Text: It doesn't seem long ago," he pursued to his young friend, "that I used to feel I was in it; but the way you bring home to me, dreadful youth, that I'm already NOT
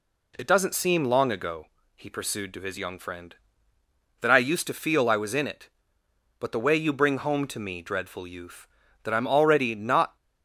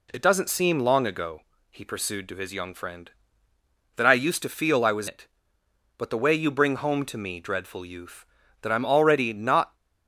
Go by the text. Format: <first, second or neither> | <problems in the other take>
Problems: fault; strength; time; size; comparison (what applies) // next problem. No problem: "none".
first | skips "in"; at 5.0 s